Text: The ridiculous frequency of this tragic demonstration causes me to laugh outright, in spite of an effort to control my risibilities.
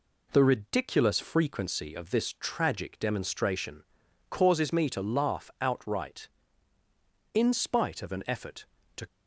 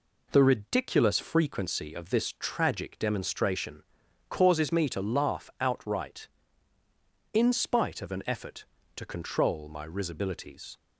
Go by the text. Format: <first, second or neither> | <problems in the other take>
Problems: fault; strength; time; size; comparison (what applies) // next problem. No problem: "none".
second | pauses between "demonstration" and "causes"; noticeable; at 3.8 s; 0.46 s long; noticeable in the second // stops before "control my risibilities"; at 9.0 s